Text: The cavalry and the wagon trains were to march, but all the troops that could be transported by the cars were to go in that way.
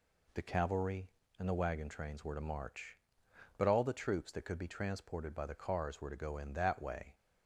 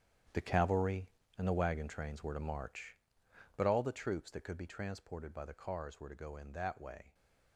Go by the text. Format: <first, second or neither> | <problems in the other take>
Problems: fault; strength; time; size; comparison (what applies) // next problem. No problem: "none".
first | gets quieter; strong; throughout; 13 dB